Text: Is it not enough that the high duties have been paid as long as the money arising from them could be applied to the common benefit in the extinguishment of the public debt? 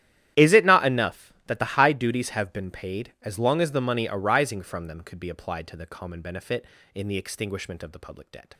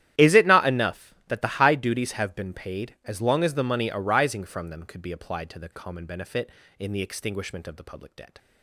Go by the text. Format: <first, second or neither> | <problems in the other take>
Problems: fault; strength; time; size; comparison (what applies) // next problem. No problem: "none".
neither | starts louder than the rest; strong; the same in both